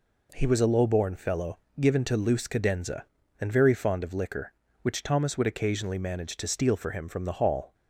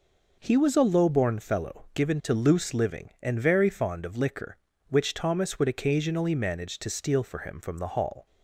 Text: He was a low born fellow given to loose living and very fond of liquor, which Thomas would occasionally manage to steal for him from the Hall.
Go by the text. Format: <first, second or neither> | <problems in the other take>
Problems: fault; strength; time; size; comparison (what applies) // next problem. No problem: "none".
second | pauses between "fellow" and "given"; slight; at 1.5 s; 0.22 s long // says "cadenza" for "living"; at 2.4 s